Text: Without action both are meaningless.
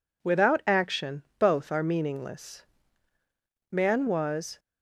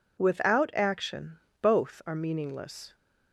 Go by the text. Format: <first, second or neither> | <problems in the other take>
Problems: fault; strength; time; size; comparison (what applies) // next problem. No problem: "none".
second | pauses between "action" and "both"; slight; at 1.2 s; 0.16 s long; slight in the second // goes on to say "Man was"; noticeable; from 3.7 s on; 0.86 s long